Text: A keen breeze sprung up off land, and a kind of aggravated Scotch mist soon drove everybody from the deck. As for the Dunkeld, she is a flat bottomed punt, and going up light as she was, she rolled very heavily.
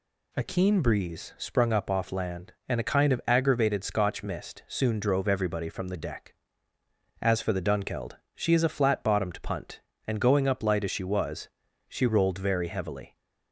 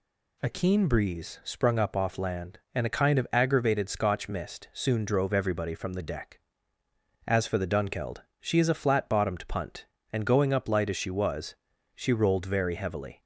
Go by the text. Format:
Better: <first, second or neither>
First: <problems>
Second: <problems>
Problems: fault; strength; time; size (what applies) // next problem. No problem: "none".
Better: neither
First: none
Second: none